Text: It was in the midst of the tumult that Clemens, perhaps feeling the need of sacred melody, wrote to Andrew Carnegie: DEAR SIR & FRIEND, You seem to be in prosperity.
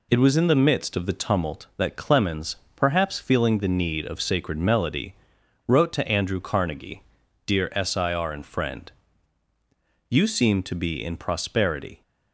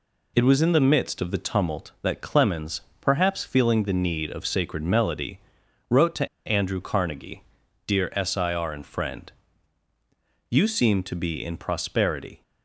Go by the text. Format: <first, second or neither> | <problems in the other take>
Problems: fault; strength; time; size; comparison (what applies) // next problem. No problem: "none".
first | pauses between "to" and "Andrew"; slight; at 6.2 s; 0.18 s long